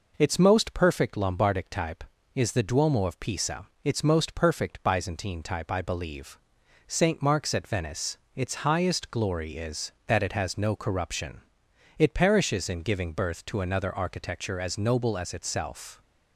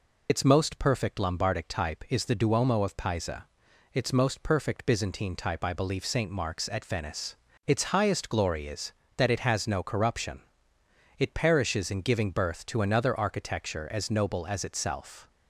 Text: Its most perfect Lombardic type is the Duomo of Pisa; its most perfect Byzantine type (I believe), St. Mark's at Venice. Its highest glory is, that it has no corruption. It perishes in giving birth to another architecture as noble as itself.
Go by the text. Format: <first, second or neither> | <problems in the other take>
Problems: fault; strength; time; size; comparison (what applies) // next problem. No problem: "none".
first | loses the start of "Its"; at 0.2 s; 40 ms